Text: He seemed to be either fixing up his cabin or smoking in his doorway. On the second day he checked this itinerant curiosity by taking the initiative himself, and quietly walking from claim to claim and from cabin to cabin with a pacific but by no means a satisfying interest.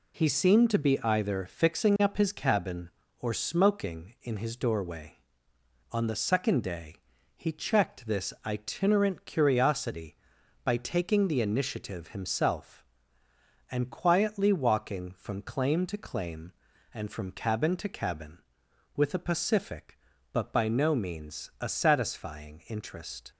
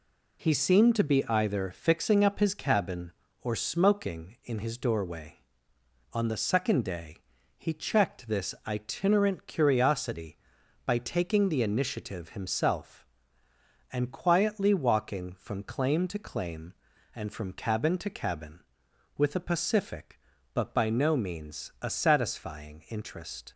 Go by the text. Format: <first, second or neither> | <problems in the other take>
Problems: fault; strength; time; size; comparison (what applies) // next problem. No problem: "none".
neither | pauses between "day" and "he"; the same in both